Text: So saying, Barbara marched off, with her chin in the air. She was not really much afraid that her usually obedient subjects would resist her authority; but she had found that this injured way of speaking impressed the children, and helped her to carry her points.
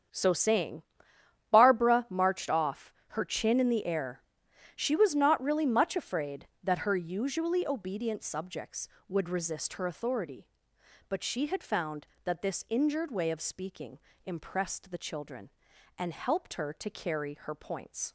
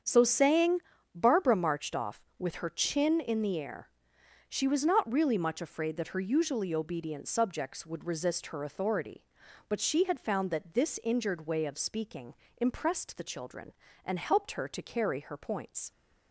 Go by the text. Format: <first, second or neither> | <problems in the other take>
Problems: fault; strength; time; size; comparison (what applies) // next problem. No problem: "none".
second | starts louder than the rest; strong; until 1.7 s; 8 dB; strong in the second // skips "with"; at 3.0 s // pauses between "speaking" and "impressed"; slight; at 13.9 s; 0.26 s long; slight in the second